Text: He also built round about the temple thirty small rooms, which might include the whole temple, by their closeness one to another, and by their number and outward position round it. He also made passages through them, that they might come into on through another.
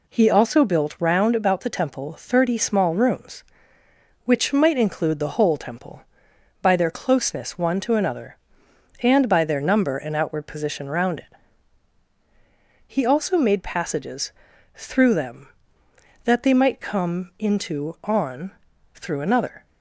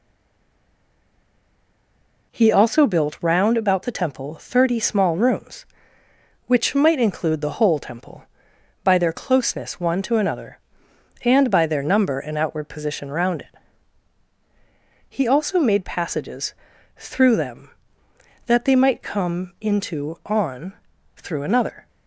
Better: first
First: pauses between "passages" and "through"; at 14.3 s; 0.44 s long // pauses between "on" and "through"; at 18.5 s; 0.44 s long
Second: stays silent before the first word; until 2.3 s; 2.3 s long // pauses between "passages" and "through"; at 16.5 s; 0.44 s long // pauses between "on" and "through"; at 20.7 s; 0.44 s long

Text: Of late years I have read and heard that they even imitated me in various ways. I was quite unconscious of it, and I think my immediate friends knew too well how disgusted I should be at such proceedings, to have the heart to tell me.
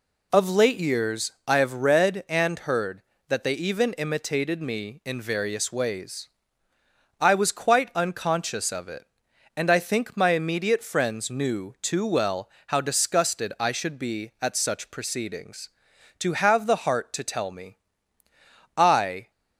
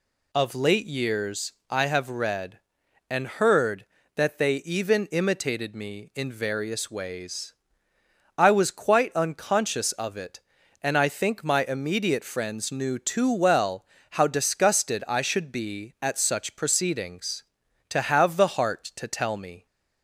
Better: second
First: pauses between "years" and "I"; slight; at 1.3 s; 0.16 s long // pauses between "well" and "how"; slight; at 12.4 s; 0.20 s long // goes on to say "I"; from 18.7 s on; 0.54 s long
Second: pauses between "years" and "I"; slight; at 1.5 s; 0.16 s long // pauses between "well" and "how"; slight; at 13.8 s; 0.26 s long

